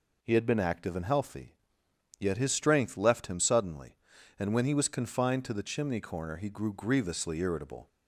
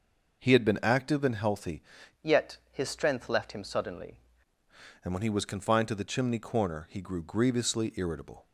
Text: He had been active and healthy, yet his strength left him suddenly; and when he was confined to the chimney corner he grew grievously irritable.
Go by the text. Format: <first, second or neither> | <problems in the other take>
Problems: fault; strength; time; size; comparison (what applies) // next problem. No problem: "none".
first | changes voice from "yet" to "suddenly"; from 2.2 to 4.1 s; 1.9 s long